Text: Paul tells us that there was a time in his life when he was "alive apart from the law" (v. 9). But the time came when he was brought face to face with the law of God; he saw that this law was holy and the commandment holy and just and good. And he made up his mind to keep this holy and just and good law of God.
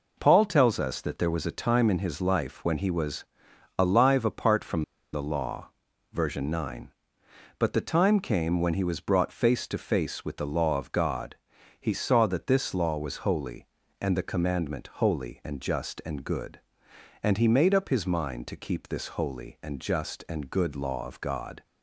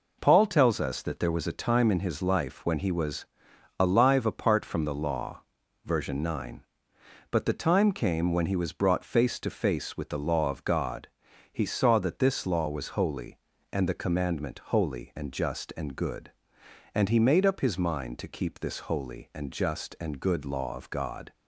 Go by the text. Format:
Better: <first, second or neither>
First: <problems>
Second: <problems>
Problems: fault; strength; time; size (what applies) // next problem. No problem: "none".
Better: second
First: pauses between "was" and "alive"; noticeable; at 3.2 s; 0.54 s long // pauses between "from" and "the"; slight; at 4.8 s; 0.31 s long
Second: pauses between "was" and "alive"; noticeable; at 3.2 s; 0.54 s long